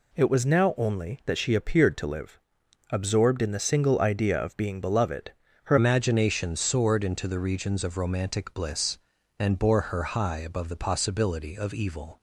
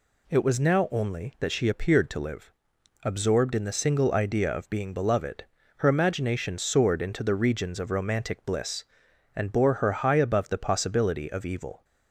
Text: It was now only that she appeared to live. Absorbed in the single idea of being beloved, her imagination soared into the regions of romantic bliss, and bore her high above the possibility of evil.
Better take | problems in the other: second | changes voice at "imagination"; from 5.7 s on; 6.5 s long

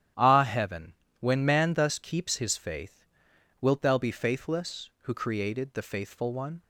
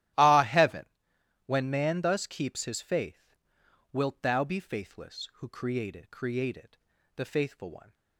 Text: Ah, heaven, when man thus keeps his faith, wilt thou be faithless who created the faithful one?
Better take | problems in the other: first | starts louder than the rest; strong; until 1.7 s; 14 dB; strong in the first // says "created" twice; at 6.1 s

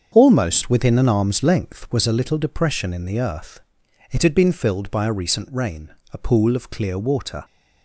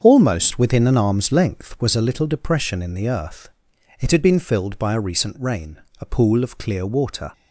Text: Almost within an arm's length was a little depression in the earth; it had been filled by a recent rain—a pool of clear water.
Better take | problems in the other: neither | starts louder than the rest; the same in both

